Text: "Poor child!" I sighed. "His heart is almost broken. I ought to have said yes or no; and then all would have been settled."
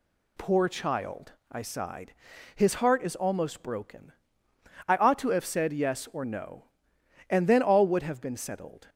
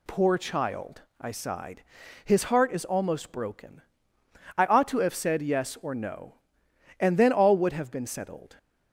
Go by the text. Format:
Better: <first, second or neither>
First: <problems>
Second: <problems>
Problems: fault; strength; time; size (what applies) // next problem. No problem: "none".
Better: neither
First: none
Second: none